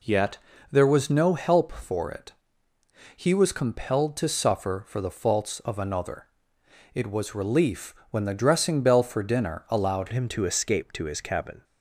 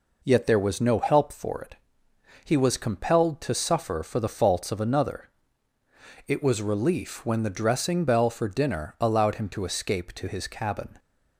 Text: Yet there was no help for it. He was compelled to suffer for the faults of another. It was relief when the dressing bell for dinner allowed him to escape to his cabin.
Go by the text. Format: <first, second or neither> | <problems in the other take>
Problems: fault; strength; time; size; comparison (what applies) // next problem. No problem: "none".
second | pauses between "Yet" and "there"; slight; at 0.3 s; 0.32 s long // pauses between "relief" and "when"; slight; at 7.9 s; 0.16 s long // changes voice at "him"; from 10.1 s on; 1.5 s long